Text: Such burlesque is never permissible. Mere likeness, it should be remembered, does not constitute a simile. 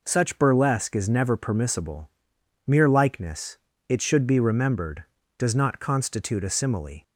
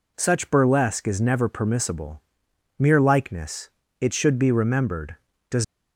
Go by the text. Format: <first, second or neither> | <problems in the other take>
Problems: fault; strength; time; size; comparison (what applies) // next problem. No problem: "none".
first | stops before "not constitute a simile"; at 5.6 s